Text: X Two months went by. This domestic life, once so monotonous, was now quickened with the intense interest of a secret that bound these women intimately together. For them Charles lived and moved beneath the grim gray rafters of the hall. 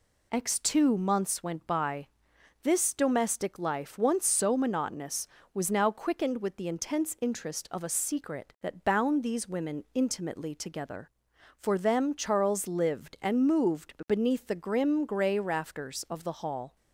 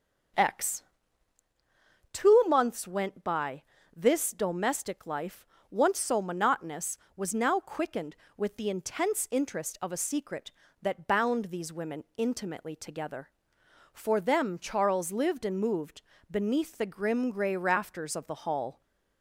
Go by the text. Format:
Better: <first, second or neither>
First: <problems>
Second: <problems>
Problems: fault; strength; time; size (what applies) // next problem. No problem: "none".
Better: first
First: pauses between "moved" and "beneath"; slight; at 13.9 s; 0.16 s long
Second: starts louder than the rest; until 1.5 s; 7 dB // pauses between "X" and "Two"; strong; at 0.8 s; 1.3 s long // pauses between "moved" and "beneath"; slight; at 16.0 s; 0.28 s long